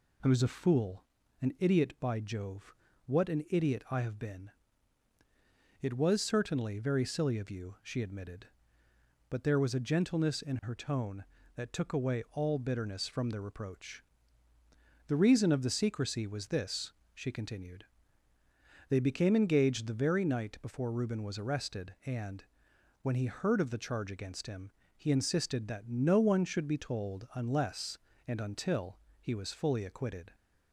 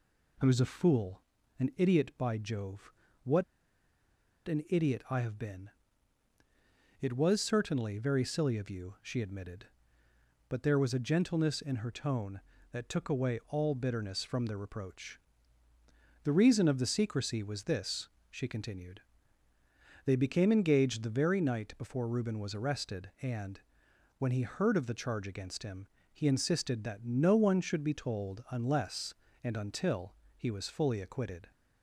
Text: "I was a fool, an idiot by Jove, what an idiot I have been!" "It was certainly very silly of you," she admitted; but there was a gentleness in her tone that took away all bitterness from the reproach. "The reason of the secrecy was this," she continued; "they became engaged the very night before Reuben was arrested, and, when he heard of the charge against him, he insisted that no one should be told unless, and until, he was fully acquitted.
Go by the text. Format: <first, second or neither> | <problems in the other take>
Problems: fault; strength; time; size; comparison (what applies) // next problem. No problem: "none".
first | pauses between "what" and "an"; at 3.4 s; 1.0 s long